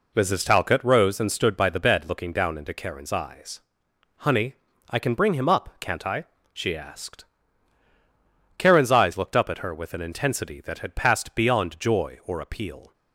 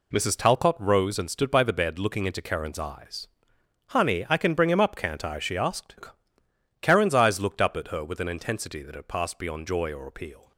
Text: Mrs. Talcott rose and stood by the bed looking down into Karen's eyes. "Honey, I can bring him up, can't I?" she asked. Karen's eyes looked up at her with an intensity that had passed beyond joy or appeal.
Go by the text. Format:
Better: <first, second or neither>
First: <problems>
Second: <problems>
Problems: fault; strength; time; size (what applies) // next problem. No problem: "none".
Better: first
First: none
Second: skips "down"; at 2.2 s